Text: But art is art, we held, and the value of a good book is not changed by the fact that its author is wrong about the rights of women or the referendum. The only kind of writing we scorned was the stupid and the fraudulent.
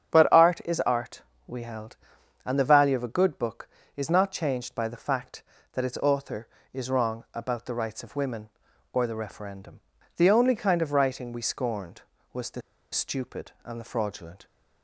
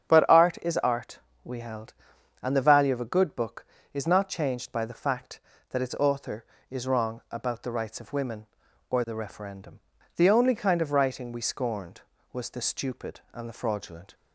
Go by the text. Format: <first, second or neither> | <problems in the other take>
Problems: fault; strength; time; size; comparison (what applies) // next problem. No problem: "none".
second | starts louder than the rest; strong; until 1.1 s; 8.5 dB; strong in the second // pauses between "the" and "stupid"; slight; at 12.6 s; 0.32 s long